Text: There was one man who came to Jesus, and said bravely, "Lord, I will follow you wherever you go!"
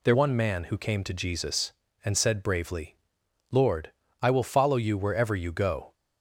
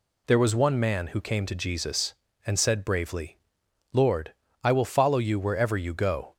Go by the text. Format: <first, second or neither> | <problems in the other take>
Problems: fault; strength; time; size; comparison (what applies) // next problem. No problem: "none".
second | skips "was"; at 0.1 s